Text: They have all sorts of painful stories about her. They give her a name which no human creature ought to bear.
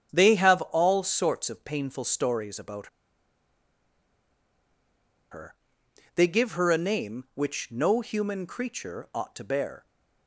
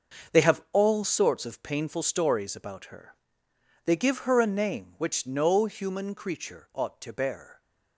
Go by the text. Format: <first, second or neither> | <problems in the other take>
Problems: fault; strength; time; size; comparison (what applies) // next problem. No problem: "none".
second | starts louder than the rest; strong; until 1.1 s; 8 dB; also in the second // pauses between "about" and "her"; strong; at 2.8 s; 2.4 s long